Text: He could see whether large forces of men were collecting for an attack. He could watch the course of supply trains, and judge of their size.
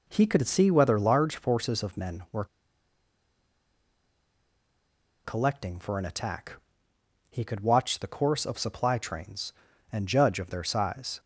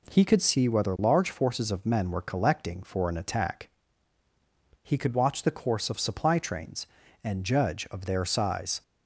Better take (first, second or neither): second